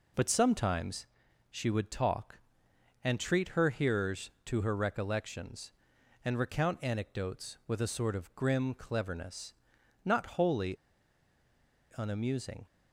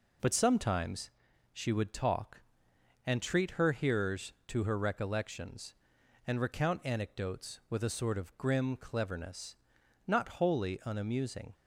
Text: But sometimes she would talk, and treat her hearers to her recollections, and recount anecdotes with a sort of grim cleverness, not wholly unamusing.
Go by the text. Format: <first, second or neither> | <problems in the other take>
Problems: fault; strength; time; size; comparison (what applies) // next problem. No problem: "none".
second | pauses between "sometimes" and "she"; noticeable; at 1.0 s; 0.46 s long; also in the second // pauses between "wholly" and "unamusing"; at 10.7 s; 1.2 s long